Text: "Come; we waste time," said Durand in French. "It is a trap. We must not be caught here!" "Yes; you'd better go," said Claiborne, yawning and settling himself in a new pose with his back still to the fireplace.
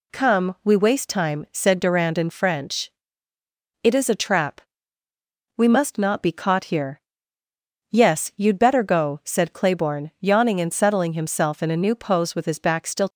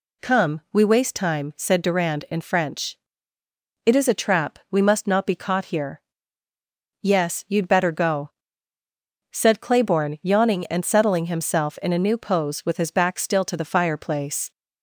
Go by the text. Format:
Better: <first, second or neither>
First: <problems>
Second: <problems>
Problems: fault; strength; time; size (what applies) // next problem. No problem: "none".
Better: second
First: stops before "to the fireplace"; at 13.0 s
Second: none